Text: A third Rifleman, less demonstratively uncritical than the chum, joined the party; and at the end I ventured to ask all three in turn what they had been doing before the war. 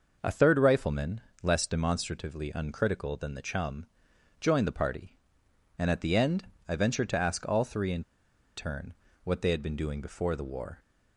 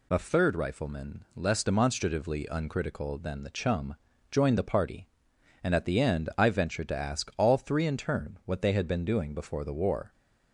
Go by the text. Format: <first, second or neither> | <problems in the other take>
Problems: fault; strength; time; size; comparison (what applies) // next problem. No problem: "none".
second | pauses between "end" and "I"; slight; at 6.4 s; 0.22 s long // pauses between "in" and "turn"; noticeable; at 8.0 s; 0.53 s long // pauses between "turn" and "what"; slight; at 8.9 s; 0.32 s long